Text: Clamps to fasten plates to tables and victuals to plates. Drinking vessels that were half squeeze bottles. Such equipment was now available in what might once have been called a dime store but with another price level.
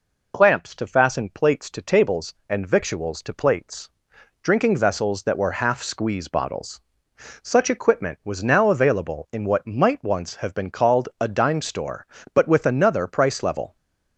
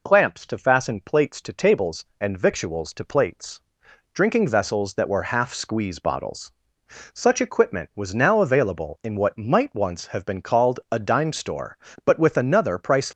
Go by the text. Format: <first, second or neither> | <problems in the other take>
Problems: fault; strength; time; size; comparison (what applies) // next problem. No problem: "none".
first | stops before "level"; at 13.0 s